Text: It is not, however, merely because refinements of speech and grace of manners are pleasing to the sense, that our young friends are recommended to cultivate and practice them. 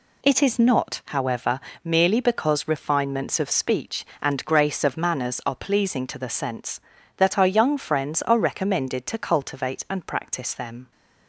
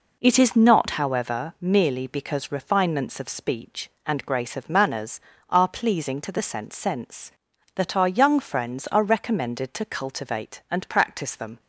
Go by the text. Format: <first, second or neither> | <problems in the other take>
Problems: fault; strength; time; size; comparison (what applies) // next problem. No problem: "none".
first | says "sense" twice; at 6.7 s